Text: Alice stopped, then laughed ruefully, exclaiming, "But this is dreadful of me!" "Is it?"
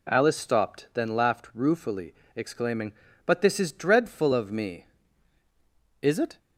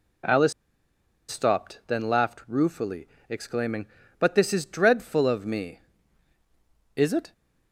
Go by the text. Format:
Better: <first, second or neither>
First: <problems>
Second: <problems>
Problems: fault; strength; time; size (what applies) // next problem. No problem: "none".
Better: first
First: none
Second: pauses between "Alice" and "stopped"; noticeable; at 0.5 s; 0.77 s long